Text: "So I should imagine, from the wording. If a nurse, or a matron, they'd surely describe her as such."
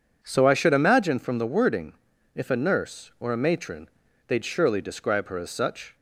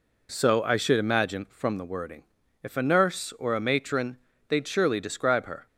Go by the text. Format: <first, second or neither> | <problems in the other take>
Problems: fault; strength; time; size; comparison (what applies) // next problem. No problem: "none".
first | stops before "as such"; at 5.6 s